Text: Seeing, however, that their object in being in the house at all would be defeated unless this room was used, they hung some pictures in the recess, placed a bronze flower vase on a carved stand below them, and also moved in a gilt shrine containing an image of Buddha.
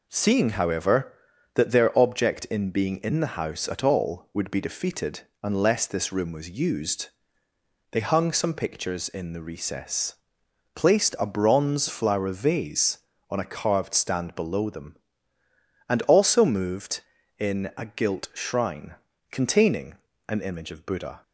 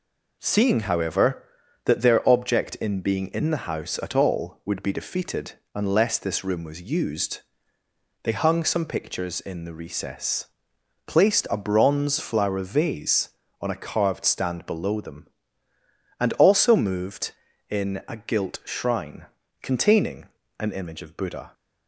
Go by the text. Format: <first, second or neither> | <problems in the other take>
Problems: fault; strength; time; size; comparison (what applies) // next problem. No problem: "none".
neither | pauses between "defeated" and "unless"; slight; the same in both // pauses between "shrine" and "containing"; slight; the same in both // pauses between "containing" and "an"; slight; the same in both